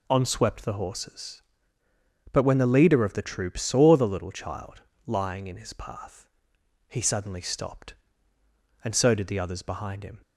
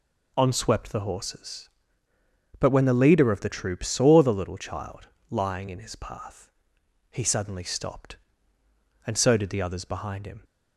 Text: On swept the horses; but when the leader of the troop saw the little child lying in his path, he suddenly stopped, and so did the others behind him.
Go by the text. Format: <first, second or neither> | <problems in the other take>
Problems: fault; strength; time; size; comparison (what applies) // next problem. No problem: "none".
neither | pauses between "child" and "lying"; slight; the same in both